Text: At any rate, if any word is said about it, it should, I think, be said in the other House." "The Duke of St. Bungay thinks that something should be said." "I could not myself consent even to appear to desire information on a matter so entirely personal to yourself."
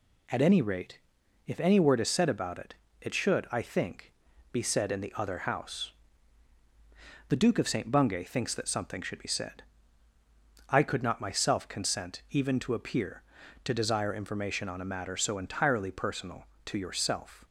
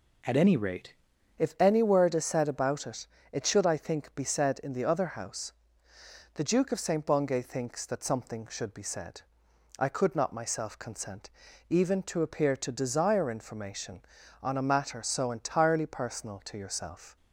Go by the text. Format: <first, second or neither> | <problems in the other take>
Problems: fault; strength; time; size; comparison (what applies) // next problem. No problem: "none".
first | changes voice at "if"; from 1.3 s on; 15.8 s long // pauses between "consent" and "even"; at 11.2 s; 0.40 s long